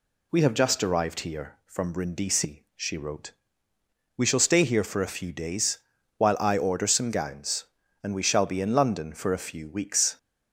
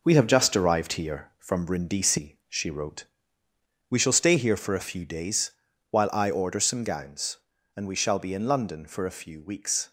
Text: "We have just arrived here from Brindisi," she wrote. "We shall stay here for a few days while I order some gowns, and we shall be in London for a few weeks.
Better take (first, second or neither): first